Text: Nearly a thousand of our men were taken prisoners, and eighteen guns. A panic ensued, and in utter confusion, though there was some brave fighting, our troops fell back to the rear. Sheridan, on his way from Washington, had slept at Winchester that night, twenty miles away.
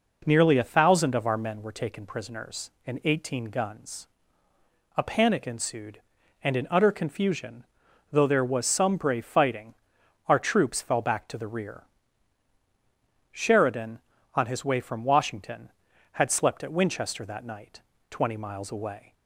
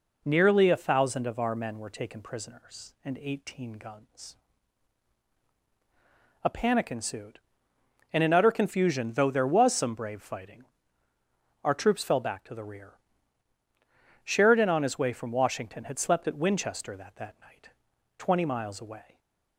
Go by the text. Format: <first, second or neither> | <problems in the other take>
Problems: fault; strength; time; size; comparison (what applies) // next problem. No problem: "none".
first | says "that" twice; at 17.1 s